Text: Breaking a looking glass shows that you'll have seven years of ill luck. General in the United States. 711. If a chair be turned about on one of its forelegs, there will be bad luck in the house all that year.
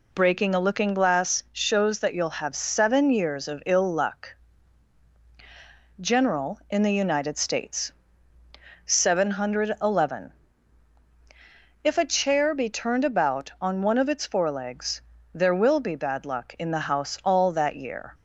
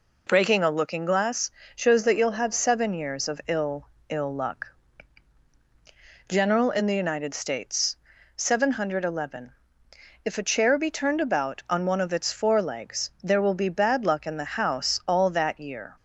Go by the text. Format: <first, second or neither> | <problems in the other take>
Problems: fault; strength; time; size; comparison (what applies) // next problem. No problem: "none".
first | pauses between "glass" and "shows"; slight; at 1.4 s; 0.24 s long // says "ill" twice; at 4.0 s